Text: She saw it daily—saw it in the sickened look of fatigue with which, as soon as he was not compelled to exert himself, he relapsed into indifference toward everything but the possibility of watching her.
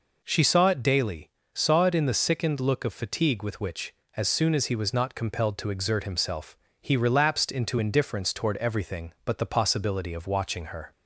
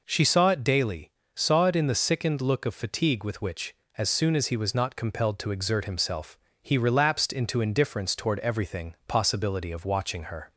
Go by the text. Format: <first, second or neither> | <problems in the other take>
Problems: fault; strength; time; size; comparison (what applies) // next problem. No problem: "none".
first | skips "but the"; at 9.0 s